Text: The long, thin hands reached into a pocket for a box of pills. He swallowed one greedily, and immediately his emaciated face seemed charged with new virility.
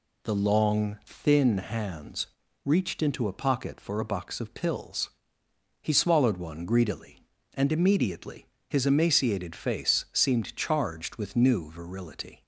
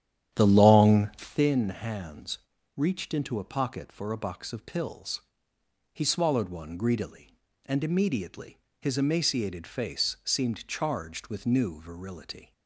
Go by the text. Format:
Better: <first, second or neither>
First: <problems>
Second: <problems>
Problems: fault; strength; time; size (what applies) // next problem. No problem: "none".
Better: first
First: pauses between "hands" and "reached"; at 2.2 s; 0.38 s long // pauses between "immediately" and "his"; slight; at 8.4 s; 0.22 s long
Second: starts louder than the rest; strong; until 1.4 s; 10 dB // pauses between "hands" and "reached"; at 2.3 s; 0.38 s long // pauses between "immediately" and "his"; slight; at 8.5 s; 0.22 s long